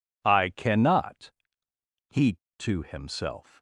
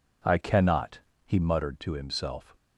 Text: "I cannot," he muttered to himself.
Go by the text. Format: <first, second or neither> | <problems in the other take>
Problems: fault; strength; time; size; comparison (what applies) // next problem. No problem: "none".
second | skips "muttered"; at 2.4 s